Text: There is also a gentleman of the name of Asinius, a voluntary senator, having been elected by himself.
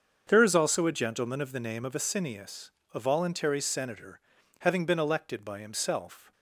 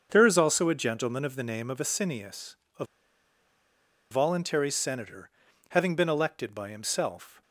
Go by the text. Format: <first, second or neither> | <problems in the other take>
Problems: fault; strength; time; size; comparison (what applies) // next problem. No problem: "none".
first | starts louder than the rest; until 1.1 s; 6.5 dB; also in the first // pauses between "a" and "voluntary"; strong; at 2.8 s; 1.2 s long